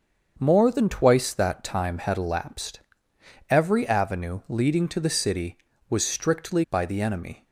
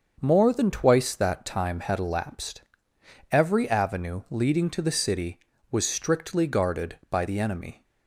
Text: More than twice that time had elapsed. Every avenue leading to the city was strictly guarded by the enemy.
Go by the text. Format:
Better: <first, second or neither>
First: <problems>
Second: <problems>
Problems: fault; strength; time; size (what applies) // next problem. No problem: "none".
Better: second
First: starts louder than the rest; until 1.3 s; 7 dB // skips "guarded"; at 6.6 s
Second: starts louder than the rest; until 1.2 s; 6.5 dB